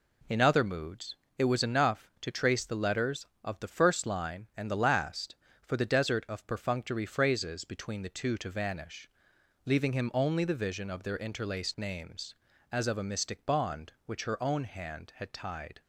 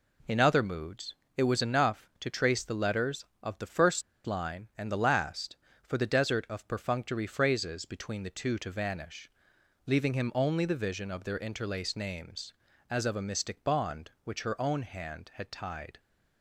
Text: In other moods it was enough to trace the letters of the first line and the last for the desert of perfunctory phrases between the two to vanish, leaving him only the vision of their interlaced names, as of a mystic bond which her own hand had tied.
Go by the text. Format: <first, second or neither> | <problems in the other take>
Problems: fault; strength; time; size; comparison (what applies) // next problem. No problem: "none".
first | pauses between "moods" and "it"; slight; at 1.1 s; 0.20 s long; slight in the first // pauses between "first" and "line"; slight; at 4.0 s; 0.24 s long